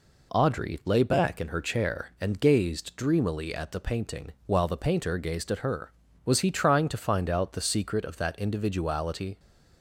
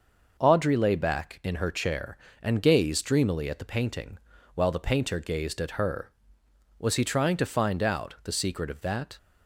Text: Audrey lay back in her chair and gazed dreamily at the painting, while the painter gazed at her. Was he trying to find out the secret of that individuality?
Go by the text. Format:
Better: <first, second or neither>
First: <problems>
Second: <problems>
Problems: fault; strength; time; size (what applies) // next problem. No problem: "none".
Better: first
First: none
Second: stops before "individuality"; at 9.1 s